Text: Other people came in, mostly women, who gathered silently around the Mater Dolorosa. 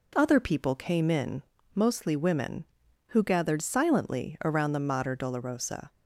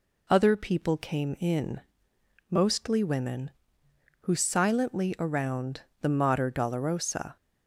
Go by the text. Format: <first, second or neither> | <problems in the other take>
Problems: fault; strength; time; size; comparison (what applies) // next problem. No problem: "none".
first | skips "gathered"; at 4.3 s // pauses between "around" and "the"; slight; at 5.8 s; 0.18 s long